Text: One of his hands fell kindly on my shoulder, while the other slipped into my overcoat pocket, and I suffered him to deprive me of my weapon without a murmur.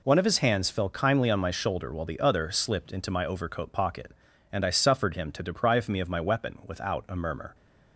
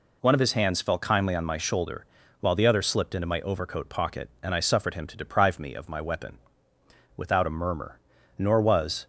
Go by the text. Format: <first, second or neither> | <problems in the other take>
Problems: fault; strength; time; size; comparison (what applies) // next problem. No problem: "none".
first | pauses between "weapon" and "without"; noticeable; at 6.3 s; 0.78 s long // goes on to say "Nor was"; noticeable; from 8.3 s on; 0.68 s long